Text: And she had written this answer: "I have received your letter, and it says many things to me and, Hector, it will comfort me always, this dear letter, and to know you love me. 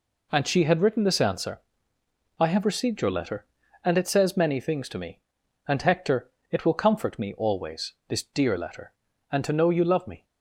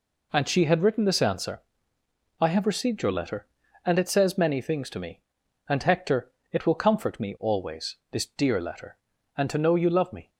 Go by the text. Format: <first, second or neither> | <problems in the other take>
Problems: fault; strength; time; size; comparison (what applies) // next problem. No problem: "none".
neither | none